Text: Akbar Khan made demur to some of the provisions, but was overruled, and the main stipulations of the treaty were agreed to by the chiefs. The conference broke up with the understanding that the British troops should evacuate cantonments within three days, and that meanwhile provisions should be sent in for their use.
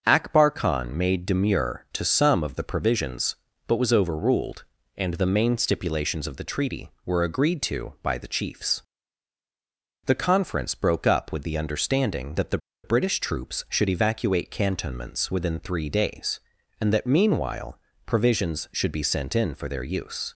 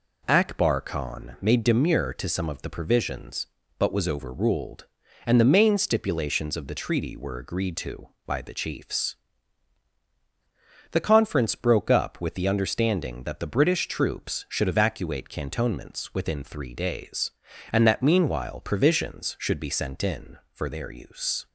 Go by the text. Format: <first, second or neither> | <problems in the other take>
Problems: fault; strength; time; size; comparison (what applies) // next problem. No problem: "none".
second | starts louder than the rest; until 1.0 s; 6.5 dB // pauses between "the" and "British"; slight; at 12.5 s; 0.26 s long // pauses between "meanwhile" and "provisions"; slight; at 17.7 s; 0.28 s long